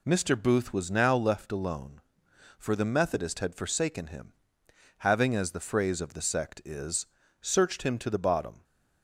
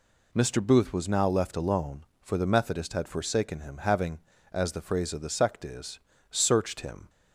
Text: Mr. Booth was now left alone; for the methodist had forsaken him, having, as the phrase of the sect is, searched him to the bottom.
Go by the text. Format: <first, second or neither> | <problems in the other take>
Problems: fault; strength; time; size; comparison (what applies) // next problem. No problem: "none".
first | stops before "to the bottom"; at 7.0 s